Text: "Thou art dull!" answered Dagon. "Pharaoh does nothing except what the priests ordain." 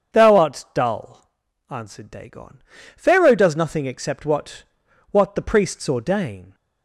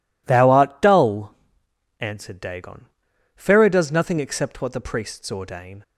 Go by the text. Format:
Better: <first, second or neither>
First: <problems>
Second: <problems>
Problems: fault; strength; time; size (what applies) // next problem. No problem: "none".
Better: second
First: starts louder than the rest; until 1.2 s; 7 dB // says "what" twice; at 5.1 s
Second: none